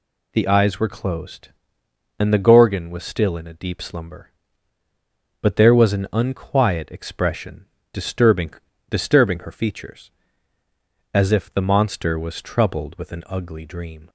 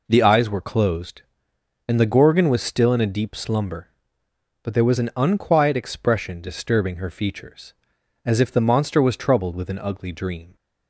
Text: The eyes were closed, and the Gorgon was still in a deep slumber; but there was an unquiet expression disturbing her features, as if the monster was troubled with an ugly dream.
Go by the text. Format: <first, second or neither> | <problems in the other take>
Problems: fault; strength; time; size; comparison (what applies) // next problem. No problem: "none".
second | pauses between "expression" and "disturbing"; slight; at 7.6 s; 0.26 s long // says "disturbing" twice; at 8.8 s